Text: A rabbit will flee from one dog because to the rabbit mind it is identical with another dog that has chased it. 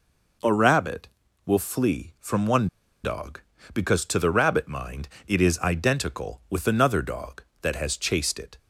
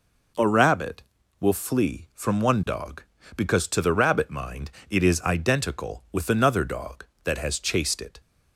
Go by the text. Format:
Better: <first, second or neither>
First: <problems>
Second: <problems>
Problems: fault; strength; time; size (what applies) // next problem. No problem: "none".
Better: second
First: pauses between "one" and "dog"; slight; at 2.6 s; 0.34 s long // pauses between "mind" and "it"; slight; at 5.0 s; 0.20 s long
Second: pauses between "mind" and "it"; slight; at 4.7 s; 0.20 s long